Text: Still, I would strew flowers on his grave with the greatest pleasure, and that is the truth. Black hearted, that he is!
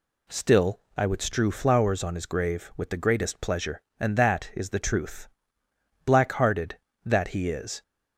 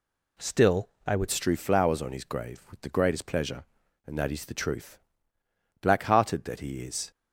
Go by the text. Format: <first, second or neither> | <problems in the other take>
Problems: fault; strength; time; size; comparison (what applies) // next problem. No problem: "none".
first | changes voice at "strew"; from 1.3 s on; 5.8 s long